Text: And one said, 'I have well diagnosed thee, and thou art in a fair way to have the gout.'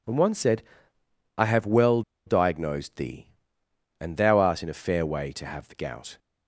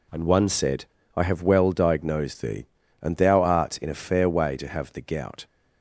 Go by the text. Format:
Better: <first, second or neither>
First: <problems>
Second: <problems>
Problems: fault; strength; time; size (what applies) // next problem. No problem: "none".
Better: second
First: pauses between "well" and "diagnosed"; slight; at 2.0 s; 0.24 s long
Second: none